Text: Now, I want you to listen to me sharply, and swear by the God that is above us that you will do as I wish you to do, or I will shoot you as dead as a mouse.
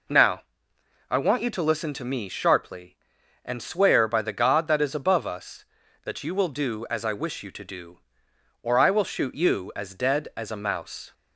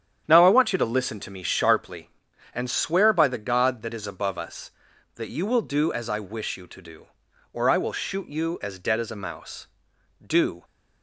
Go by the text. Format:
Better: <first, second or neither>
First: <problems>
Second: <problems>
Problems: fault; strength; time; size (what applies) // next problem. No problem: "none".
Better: first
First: none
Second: starts louder than the rest; strong; until 1.2 s; 9 dB // goes on to say "Do"; slight; from 10.2 s on; 0.40 s long